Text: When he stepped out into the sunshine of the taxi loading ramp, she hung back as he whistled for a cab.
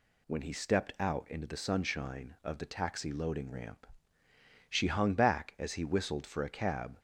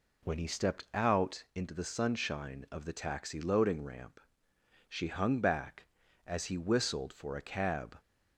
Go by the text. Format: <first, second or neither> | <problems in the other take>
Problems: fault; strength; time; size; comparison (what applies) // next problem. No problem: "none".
neither | none